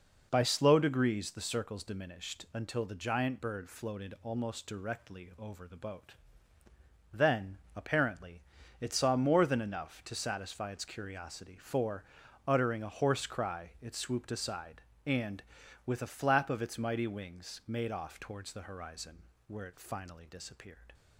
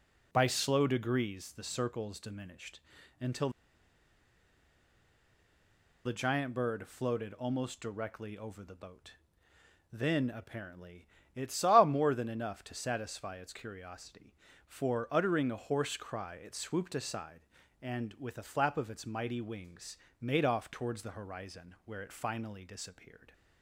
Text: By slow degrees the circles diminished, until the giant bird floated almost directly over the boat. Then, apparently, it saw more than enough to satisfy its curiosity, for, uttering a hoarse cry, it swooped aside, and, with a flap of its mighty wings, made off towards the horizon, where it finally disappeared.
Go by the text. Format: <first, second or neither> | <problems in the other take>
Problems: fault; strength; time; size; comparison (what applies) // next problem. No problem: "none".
first | pauses between "until" and "the"; strong; at 3.4 s; 2.5 s long